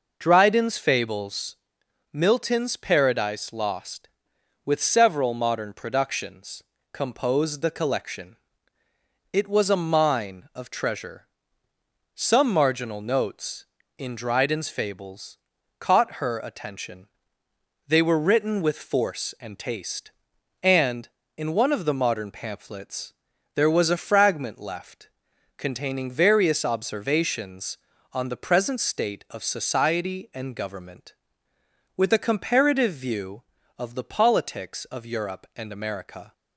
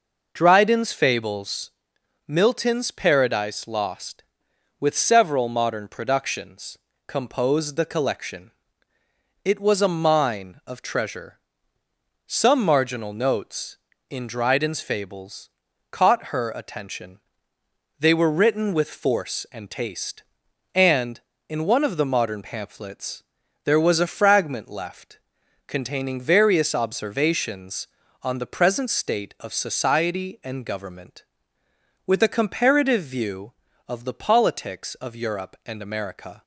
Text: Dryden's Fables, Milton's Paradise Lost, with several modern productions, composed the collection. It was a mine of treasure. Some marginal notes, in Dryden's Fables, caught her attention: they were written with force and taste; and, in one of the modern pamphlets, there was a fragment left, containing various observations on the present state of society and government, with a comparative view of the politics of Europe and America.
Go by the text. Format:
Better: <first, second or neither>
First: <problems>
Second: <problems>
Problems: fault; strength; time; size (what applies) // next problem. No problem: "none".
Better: neither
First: none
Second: none